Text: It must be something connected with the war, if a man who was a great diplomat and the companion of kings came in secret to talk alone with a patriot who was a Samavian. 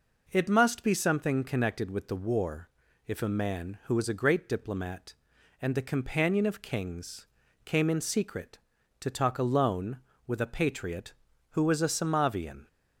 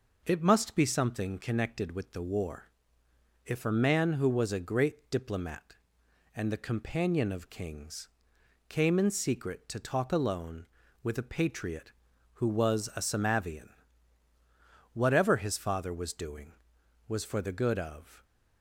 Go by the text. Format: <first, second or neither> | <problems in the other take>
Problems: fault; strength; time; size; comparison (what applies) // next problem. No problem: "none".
first | pauses between "kings" and "came"; noticeable; at 8.0 s; 0.62 s long; slight in the first // goes on to say "Whatever his father was doing was for the good of"; strong; from 14.9 s on; 3.3 s long